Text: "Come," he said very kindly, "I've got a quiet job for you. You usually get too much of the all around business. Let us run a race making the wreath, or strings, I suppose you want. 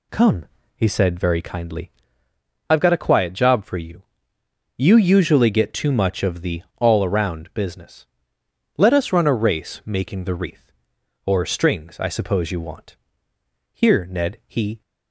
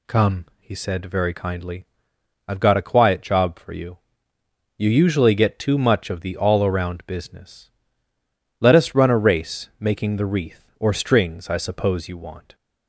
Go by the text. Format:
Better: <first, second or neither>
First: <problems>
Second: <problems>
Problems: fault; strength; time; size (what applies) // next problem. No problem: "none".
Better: second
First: goes on to say "Here Ned he"; noticeable; from 13.7 s on; 1.1 s long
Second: none